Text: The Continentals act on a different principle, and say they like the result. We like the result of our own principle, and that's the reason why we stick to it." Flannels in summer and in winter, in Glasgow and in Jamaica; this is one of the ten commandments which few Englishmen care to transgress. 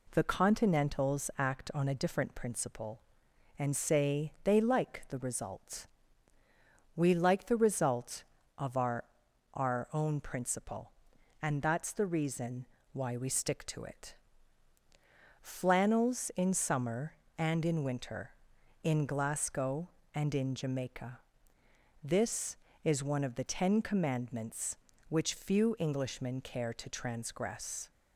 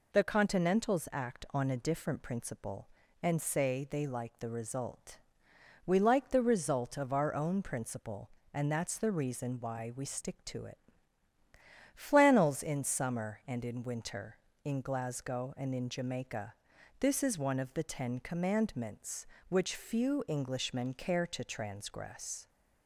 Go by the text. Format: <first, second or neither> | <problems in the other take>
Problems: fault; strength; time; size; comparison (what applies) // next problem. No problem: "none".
second | says "our" twice; at 9.5 s // pauses between "reason" and "why"; slight; at 12.6 s; 0.28 s long